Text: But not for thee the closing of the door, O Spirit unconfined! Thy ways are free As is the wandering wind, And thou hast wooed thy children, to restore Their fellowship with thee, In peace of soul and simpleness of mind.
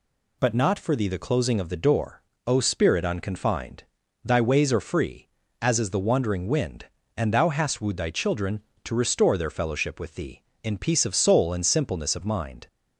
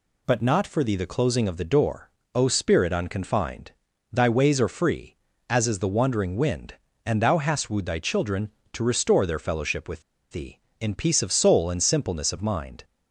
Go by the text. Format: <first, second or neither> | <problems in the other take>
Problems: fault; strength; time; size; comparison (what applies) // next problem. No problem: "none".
first | pauses between "with" and "thee"; slight; at 10.0 s; 0.29 s long